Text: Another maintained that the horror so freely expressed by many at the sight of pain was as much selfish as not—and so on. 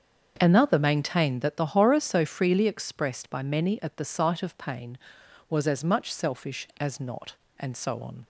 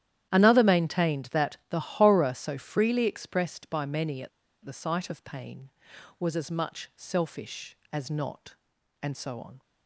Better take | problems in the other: first | starts louder than the rest; strong; until 1.3 s; 11.5 dB; also in the first // pauses between "at" and "the"; slight; at 4.2 s; 0.35 s long

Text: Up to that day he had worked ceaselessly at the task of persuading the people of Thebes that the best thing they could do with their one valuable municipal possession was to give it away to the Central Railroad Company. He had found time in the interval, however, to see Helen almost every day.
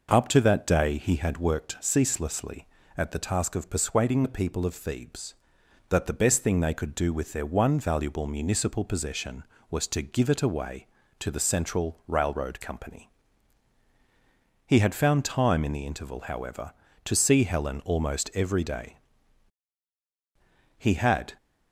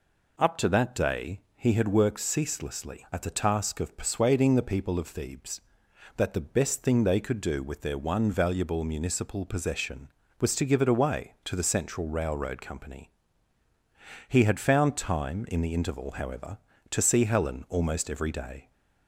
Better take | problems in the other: second | goes on to say "He had"; from 20.7 s on; 0.58 s long

